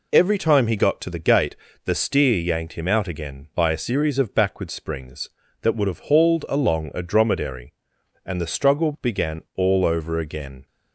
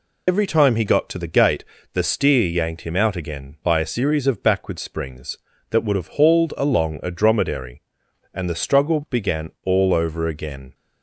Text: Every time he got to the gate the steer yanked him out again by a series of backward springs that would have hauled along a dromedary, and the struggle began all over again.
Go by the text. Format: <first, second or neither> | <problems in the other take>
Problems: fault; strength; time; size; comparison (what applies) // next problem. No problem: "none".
first | loses the start of "Every"; at 0.2 s; 75 ms // pauses between "gate" and "the"; slight; at 1.6 s; 0.28 s long; slight in the first